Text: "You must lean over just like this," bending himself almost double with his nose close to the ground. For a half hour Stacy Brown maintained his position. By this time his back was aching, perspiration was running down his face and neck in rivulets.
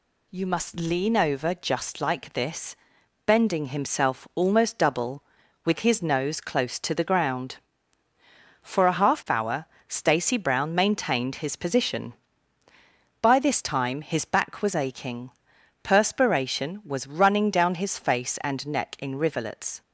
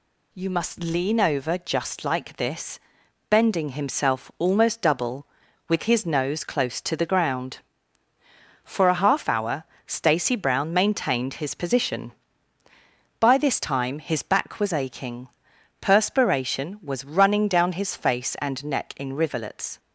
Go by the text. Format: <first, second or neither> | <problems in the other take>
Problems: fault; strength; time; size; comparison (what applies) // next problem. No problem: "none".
neither | pauses between "hour" and "Stacy"; slight; the same in both